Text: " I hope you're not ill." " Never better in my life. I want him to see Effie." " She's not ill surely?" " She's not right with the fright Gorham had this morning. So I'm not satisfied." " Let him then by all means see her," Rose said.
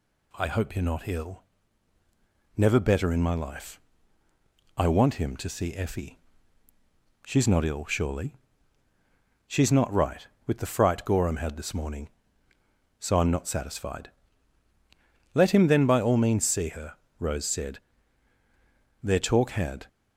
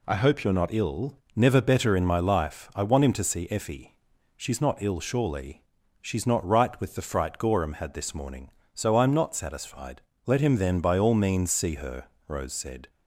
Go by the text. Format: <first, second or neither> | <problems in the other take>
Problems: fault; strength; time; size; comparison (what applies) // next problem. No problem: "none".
second | goes on to say "Their talk had"; noticeable; from 19.0 s on; 0.84 s long